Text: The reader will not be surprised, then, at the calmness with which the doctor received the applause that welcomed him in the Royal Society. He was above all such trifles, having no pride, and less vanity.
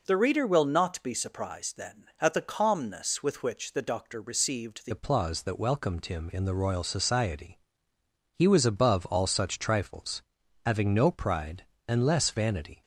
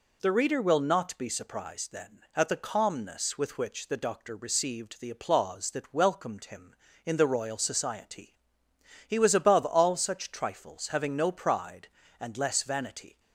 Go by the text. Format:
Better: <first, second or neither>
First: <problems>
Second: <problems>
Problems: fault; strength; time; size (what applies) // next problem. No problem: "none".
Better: second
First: changes voice at "applause"; from 4.9 s on; 7.9 s long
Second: none